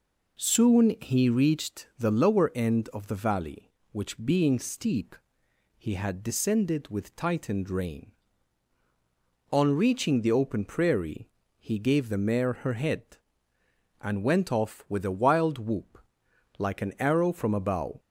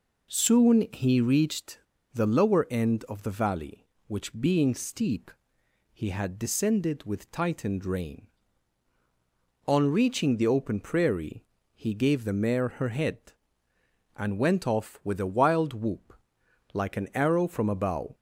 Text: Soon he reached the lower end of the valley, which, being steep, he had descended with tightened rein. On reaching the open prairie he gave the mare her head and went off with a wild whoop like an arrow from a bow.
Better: first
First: pauses between "prairie" and "he"; slight; at 11.2 s; 0.32 s long // pauses between "whoop" and "like"; noticeable; at 15.9 s; 0.62 s long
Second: pauses between "reached" and "the"; slight; at 1.7 s; 0.34 s long // pauses between "prairie" and "he"; slight; at 11.4 s; 0.32 s long // pauses between "whoop" and "like"; noticeable; at 16.1 s; 0.62 s long

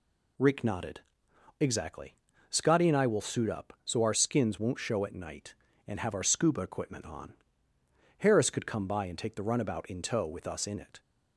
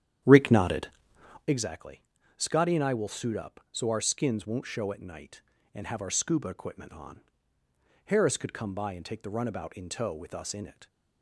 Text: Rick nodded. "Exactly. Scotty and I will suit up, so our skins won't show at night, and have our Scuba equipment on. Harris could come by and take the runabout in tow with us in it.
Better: first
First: none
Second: starts louder than the rest; strong; until 1.6 s; 10 dB

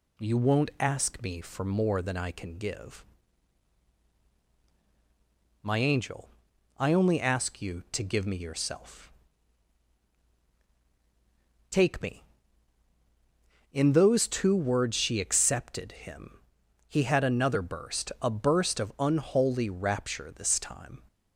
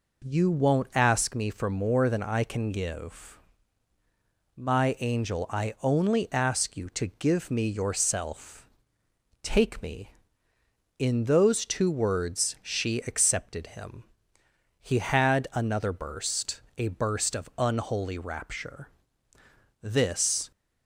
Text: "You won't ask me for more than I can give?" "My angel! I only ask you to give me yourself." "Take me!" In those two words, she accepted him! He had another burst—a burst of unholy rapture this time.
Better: first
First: none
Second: pauses between "rapture" and "this"; noticeable; at 18.8 s; 0.94 s long // stops before "time"; at 20.5 s

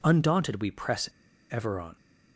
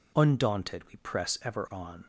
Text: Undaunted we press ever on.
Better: second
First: pauses between "press" and "ever"; at 1.0 s; 0.43 s long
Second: none

